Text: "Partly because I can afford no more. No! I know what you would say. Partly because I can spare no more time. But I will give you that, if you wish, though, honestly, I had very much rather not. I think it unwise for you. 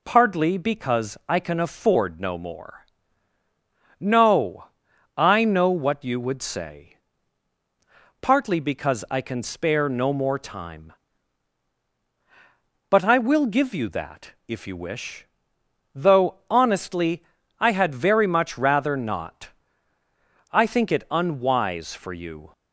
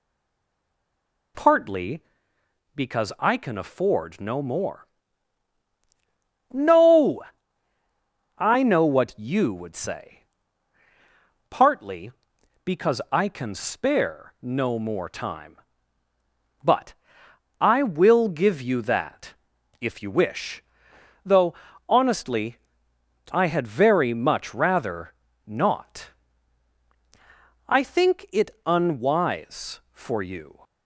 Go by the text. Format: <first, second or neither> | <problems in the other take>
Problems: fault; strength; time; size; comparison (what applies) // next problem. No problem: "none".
first | stays silent before the first word; noticeable; until 1.3 s; 1.3 s long // pauses between "But" and "I"; noticeable; at 16.9 s; 0.66 s long // pauses between "rather" and "not"; slight; at 25.1 s; 0.32 s long // pauses between "it" and "unwise"; slight; at 28.4 s; 0.16 s long